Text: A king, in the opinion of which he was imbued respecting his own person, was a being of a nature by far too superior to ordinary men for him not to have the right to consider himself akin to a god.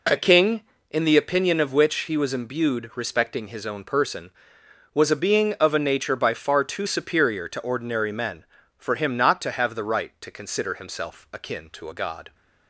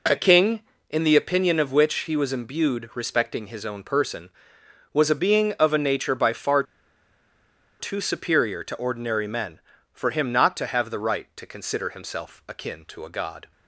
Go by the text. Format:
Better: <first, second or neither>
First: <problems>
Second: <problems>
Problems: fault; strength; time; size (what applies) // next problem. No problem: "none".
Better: first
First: none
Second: pauses between "far" and "too"; at 6.6 s; 1.1 s long